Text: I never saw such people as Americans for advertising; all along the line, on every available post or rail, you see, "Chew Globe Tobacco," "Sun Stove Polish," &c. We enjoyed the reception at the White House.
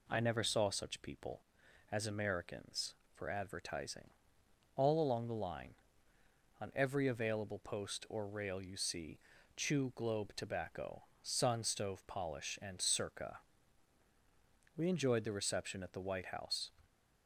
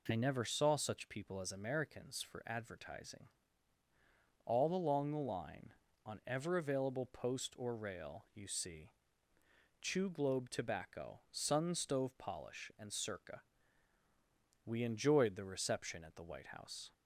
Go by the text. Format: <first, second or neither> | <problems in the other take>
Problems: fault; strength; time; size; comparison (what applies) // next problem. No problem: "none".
first | says "ever" for "every"; at 6.2 s